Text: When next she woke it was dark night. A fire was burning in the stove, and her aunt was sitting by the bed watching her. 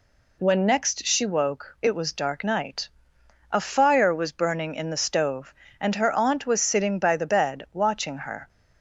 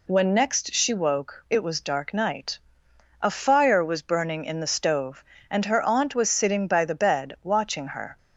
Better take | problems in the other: neither | none

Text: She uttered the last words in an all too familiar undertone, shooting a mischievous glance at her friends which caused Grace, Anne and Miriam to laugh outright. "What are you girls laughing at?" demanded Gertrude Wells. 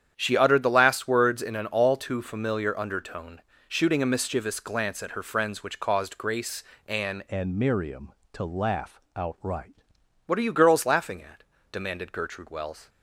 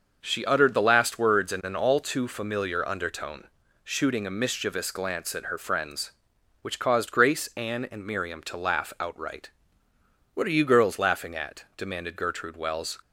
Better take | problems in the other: second | starts louder than the rest; strong; until 1.1 s; 9 dB; also in the second // changes voice from "and" to "outright"; from 7.2 to 9.7 s; 2.5 s long // pauses between "laugh" and "outright"; slight; at 9.0 s; 0.16 s long

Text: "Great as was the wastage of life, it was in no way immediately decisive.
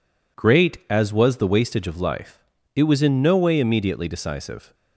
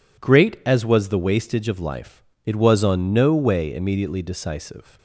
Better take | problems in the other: first | says "on" for "in"; at 2.8 s

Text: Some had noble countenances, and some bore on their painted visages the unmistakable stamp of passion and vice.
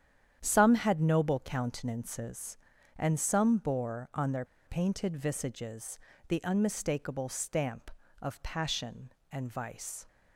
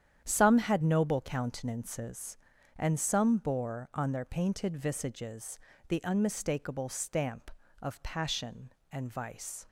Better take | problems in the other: second | starts louder than the rest; strong; until 1.4 s; 9.5 dB; strong in the second // pauses between "their" and "painted"; slight; at 4.4 s; 0.21 s long // pauses between "visages" and "the"; slight; at 5.9 s; 0.30 s long; slight in the second

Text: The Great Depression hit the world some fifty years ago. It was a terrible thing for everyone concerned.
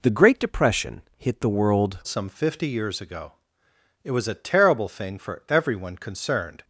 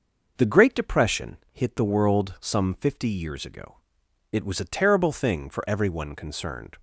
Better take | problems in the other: second | pauses between "Depression" and "hit"; slight; at 1.0 s; 0.16 s long; slight in the second // changes voice at "some"; from 2.0 s on; 4.6 s long

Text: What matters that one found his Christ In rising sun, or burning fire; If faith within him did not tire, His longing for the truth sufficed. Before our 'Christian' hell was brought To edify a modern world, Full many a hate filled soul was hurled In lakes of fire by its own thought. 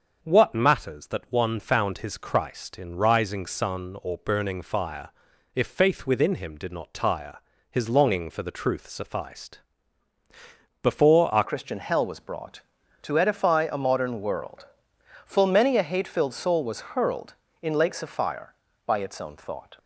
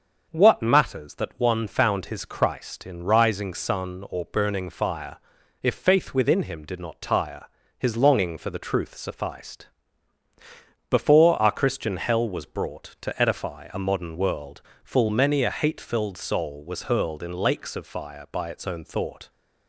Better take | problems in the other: second | starts louder than the rest; until 1.2 s; 6.5 dB; also in the second // changes voice at "Christian"; from 11.4 s on; 8.3 s long

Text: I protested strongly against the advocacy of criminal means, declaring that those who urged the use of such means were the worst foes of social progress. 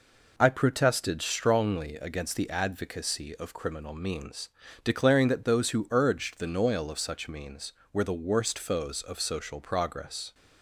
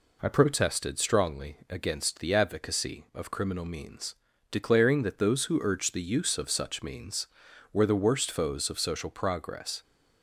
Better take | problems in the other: second | says "noil" for "use"; at 6.5 s

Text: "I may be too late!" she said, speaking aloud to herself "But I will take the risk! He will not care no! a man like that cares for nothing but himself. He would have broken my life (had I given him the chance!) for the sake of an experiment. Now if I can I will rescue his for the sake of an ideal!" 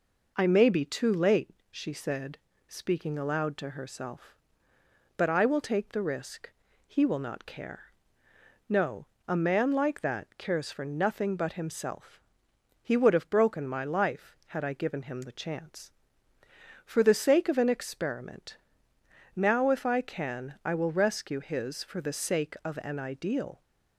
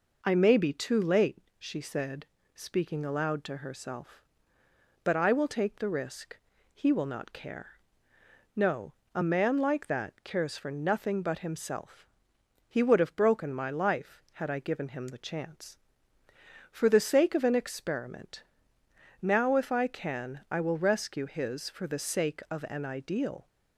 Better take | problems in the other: neither | pauses between "care" and "no"; noticeable; the same in both

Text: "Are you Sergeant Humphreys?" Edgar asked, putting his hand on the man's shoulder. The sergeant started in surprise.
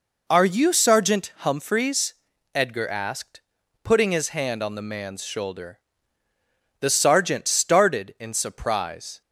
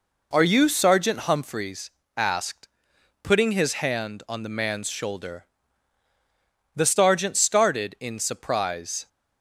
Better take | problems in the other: first | skips "Edgar"; at 2.0 s

